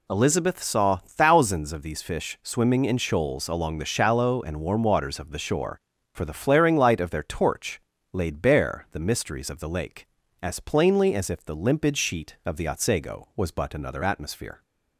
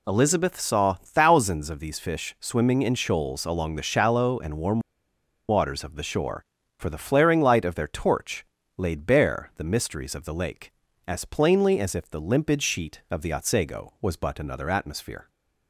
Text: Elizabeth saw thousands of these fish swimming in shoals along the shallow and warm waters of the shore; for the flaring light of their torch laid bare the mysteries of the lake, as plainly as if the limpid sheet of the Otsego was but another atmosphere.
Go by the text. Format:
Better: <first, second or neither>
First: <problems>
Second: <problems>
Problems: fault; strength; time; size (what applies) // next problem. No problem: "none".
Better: first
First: pauses between "torch" and "laid"; slight; at 7.7 s; 0.36 s long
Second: pauses between "warm" and "waters"; noticeable; at 4.7 s; 0.69 s long // pauses between "torch" and "laid"; slight; at 8.4 s; 0.36 s long